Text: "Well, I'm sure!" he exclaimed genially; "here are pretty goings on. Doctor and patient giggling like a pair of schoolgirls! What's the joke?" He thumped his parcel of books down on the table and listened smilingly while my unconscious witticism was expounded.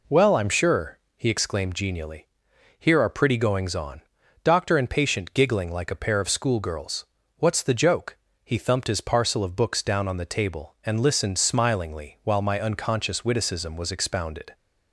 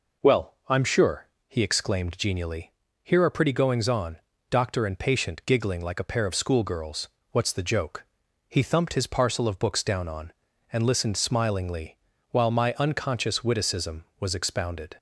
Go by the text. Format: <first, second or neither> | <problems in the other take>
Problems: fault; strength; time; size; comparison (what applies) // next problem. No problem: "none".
first | skips "the table"; at 10.5 s // pauses between "smilingly" and "while"; slight; at 11.9 s; 0.34 s long